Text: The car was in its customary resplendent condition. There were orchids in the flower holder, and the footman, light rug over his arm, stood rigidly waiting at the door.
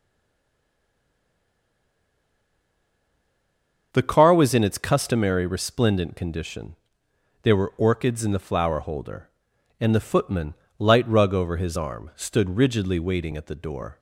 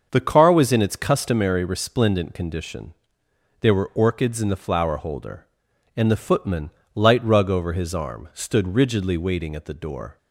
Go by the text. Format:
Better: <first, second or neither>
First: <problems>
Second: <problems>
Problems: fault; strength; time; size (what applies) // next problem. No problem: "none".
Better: second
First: stays silent before the first word; strong; until 3.9 s; 3.9 s long // starts louder than the rest; until 4.9 s; 6.5 dB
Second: starts louder than the rest; until 1.1 s; 6.5 dB